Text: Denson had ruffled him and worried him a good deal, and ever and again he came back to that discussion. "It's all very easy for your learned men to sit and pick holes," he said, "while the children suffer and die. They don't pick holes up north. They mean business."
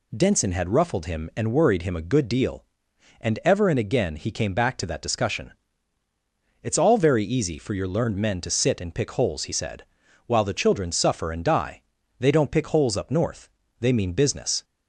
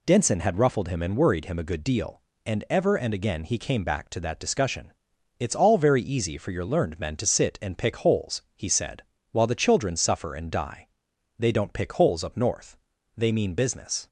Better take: neither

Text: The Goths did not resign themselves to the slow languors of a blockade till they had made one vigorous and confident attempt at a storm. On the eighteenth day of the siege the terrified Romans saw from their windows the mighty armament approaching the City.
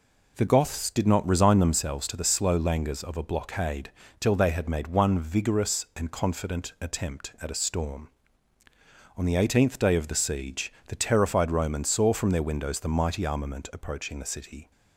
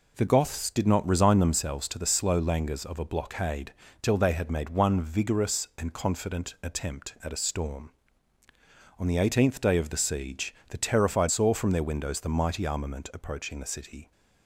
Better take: first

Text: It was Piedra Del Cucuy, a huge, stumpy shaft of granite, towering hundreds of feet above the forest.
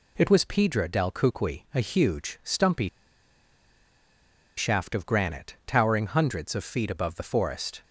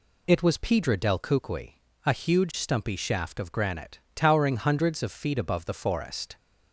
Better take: second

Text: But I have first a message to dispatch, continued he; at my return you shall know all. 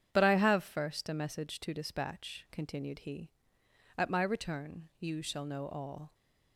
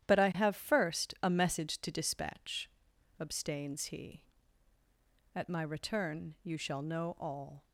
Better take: first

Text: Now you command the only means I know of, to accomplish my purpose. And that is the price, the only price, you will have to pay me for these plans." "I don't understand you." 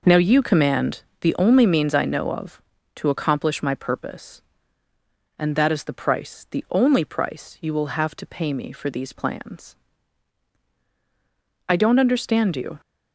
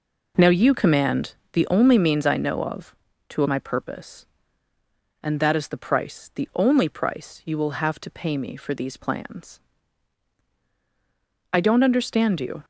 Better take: first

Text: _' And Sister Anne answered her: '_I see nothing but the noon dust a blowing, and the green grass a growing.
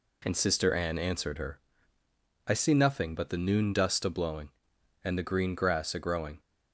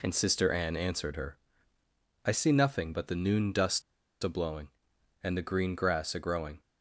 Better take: first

